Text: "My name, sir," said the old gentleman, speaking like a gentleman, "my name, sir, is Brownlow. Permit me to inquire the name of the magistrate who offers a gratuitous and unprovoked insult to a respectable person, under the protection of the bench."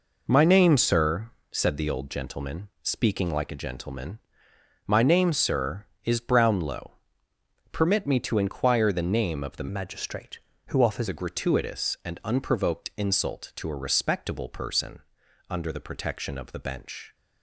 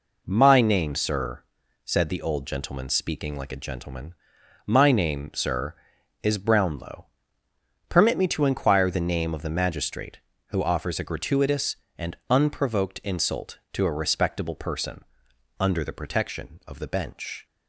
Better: second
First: changes voice from "magistrate" to "offers"; from 9.6 to 11.0 s; 1.4 s long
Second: none

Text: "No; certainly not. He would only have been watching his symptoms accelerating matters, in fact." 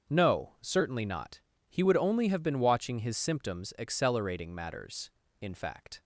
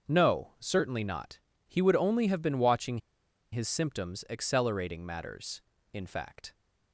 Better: first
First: starts louder than the rest; until 1.1 s; 7 dB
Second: starts louder than the rest; until 1.1 s; 7 dB // pauses between "watching" and "his"; noticeable; at 2.9 s; 0.54 s long

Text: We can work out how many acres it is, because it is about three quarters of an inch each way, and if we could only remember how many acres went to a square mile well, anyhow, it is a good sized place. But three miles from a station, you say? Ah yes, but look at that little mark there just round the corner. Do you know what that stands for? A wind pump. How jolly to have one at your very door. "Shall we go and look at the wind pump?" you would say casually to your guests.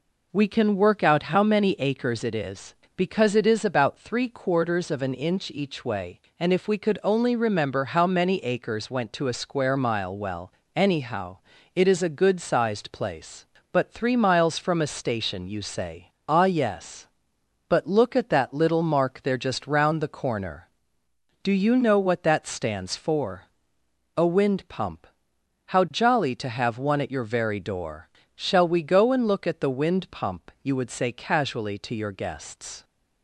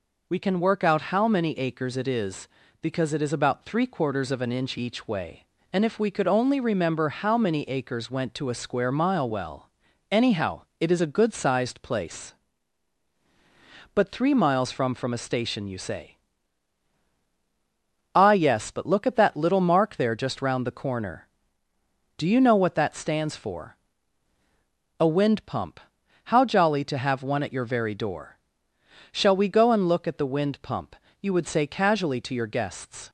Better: first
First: none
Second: says "from" twice; at 14.9 s

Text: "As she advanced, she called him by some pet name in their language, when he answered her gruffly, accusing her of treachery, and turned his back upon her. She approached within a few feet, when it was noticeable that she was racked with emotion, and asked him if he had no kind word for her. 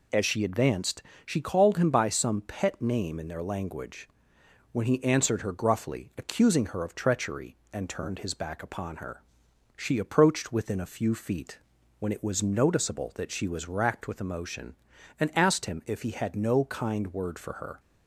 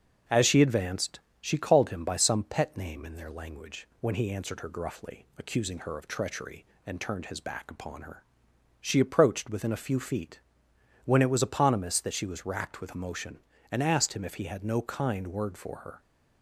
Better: first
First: none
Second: starts louder than the rest; until 1.4 s; 6.5 dB // says "eponymous" for "noticeable"; at 11.4 s

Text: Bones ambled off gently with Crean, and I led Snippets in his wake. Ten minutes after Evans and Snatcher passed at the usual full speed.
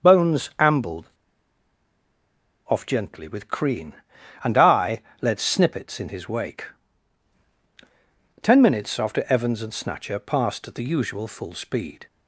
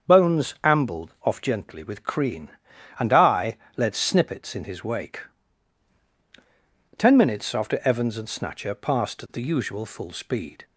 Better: second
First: starts louder than the rest; until 1.1 s; 7 dB // pauses between "ambled" and "off"; strong; at 1.0 s; 1.5 s long // pauses between "I" and "led"; slight; at 5.0 s; 0.18 s long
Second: starts louder than the rest; until 1.2 s; 7 dB // pauses between "I" and "led"; slight; at 3.5 s; 0.18 s long

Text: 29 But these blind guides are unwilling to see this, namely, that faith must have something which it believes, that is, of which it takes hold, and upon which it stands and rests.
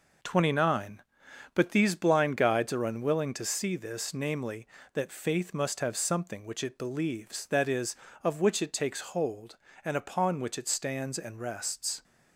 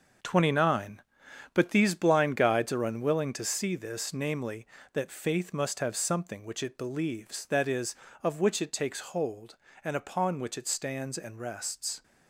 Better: first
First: none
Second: gets quieter; strong; throughout; 9 dB

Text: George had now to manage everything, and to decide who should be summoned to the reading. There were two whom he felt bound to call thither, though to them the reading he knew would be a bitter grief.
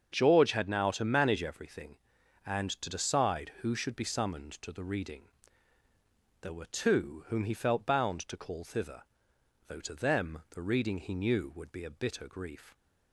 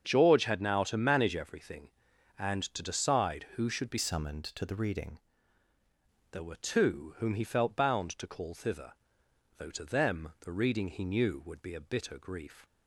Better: first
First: starts louder than the rest; until 1.1 s; 7 dB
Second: starts louder than the rest; until 1.0 s; 7 dB // changes voice from "summoned" to "reading"; from 3.9 to 5.1 s; 1.2 s long

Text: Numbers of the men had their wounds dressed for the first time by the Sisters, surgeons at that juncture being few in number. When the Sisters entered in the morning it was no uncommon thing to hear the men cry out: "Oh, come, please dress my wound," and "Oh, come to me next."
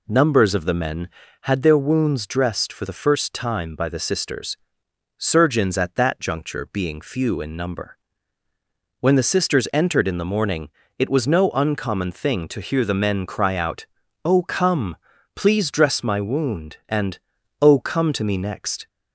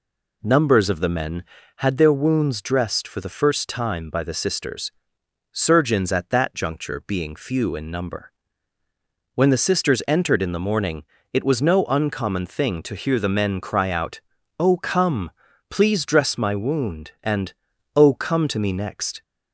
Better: neither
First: pauses between "morning" and "it"; slight; at 10.6 s; 0.32 s long // pauses between "and" and "Oh"; at 17.1 s; 0.44 s long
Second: pauses between "morning" and "it"; slight; at 11.0 s; 0.32 s long // pauses between "and" and "Oh"; at 17.5 s; 0.44 s long

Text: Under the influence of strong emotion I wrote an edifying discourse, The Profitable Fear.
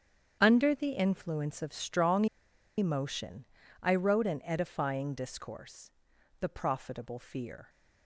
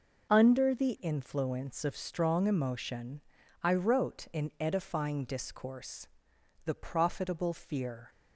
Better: second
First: starts louder than the rest; strong; until 1.4 s; 8 dB // pauses between "strong" and "emotion"; noticeable; at 2.2 s; 0.52 s long // pauses between "emotion" and "I"; slight; at 3.4 s; 0.36 s long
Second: pauses between "emotion" and "I"; at 3.2 s; 0.42 s long

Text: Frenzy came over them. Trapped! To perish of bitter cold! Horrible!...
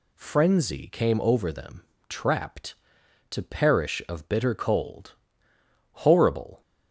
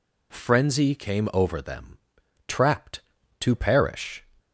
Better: first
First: none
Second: stops before "of bitter cold Horrible"; at 4.3 s

